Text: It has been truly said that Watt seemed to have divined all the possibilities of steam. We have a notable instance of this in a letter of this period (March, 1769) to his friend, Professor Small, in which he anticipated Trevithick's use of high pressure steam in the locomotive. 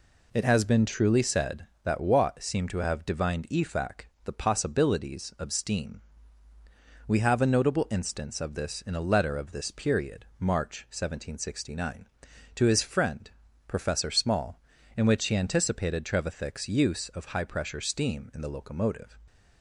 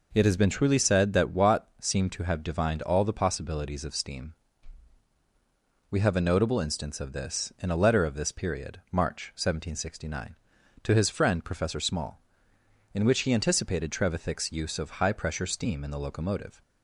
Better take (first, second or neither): second